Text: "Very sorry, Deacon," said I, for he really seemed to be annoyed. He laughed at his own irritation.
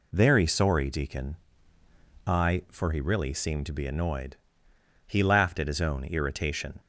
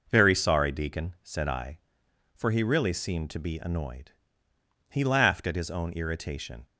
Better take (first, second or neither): second